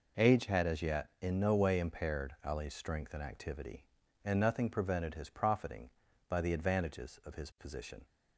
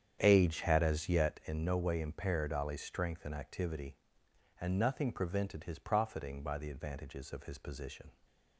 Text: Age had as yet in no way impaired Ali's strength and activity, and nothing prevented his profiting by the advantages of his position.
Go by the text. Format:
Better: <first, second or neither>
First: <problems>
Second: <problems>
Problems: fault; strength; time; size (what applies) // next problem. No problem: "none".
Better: first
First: none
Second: starts louder than the rest; strong; until 1.4 s; 8.5 dB